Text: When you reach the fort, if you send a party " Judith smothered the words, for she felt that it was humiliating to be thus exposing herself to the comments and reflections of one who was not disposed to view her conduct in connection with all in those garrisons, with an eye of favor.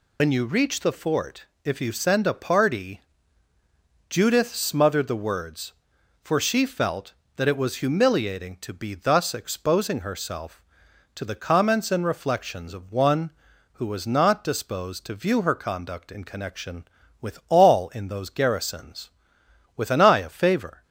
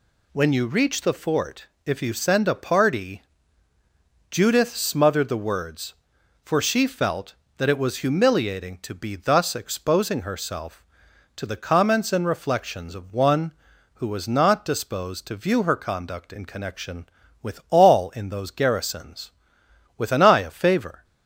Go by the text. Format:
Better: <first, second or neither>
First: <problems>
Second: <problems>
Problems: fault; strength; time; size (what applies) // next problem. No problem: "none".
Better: second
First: loses the start of "When"; at 0.1 s; 95 ms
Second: none